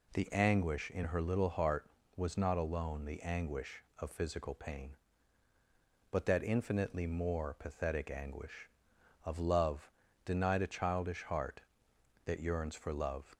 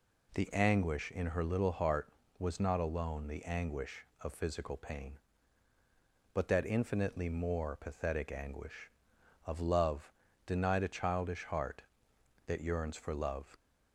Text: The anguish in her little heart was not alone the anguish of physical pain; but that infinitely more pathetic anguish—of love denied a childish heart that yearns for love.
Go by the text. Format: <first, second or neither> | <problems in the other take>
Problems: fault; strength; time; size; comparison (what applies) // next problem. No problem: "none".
neither | pauses between "love" and "denied"; slight; the same in both